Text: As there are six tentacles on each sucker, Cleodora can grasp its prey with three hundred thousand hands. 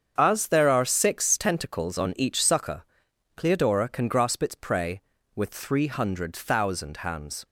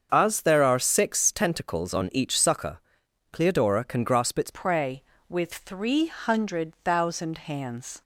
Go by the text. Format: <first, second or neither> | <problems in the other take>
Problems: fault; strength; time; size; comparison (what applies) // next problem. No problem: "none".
first | starts louder than the rest; until 1.1 s; 7 dB; strong in the first // changes voice at "prey"; from 4.5 s on; 3.5 s long